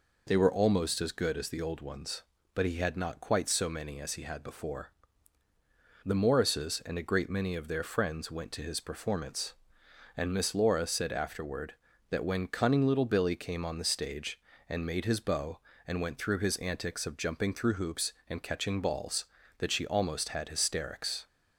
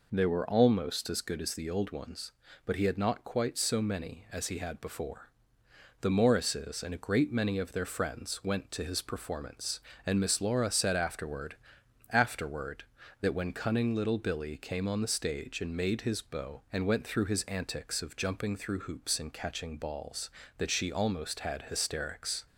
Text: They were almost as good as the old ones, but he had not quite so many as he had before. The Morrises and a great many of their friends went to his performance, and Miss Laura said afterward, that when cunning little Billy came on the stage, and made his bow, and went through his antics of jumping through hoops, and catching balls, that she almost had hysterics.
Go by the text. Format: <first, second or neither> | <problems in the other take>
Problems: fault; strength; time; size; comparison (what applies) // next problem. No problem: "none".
first | says "afterward" twice; at 12.0 s